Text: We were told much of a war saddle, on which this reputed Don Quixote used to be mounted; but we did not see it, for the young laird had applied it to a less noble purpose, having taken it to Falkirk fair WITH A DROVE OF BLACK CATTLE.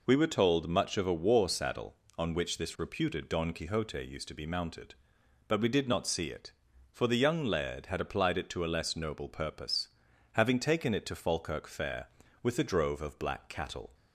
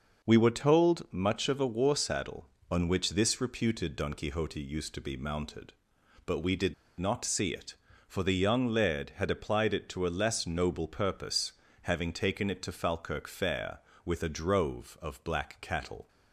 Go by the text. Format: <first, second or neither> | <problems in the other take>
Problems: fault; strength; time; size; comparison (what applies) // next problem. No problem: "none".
first | pauses between "did" and "not"; slight; at 6.7 s; 0.25 s long